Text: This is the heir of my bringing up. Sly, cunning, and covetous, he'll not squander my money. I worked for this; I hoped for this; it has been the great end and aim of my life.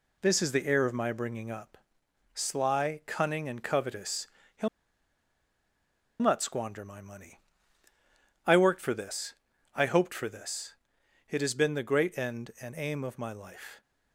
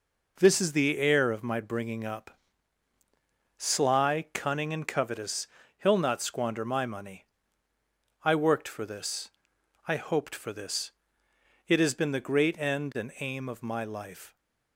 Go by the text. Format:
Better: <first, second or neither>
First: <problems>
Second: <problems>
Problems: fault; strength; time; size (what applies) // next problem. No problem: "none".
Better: second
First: pauses between "he'll" and "not"; strong; at 4.6 s; 1.5 s long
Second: none